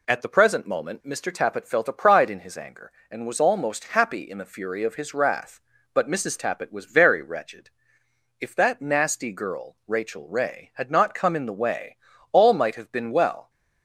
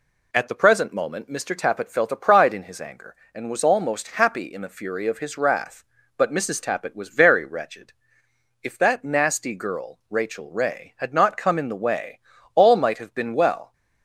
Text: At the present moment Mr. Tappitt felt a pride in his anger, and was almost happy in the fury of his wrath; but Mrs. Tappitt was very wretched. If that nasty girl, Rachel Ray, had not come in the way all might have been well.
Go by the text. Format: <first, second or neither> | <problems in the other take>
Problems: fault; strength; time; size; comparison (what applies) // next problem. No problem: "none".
neither | pauses between "way" and "all"; the same in both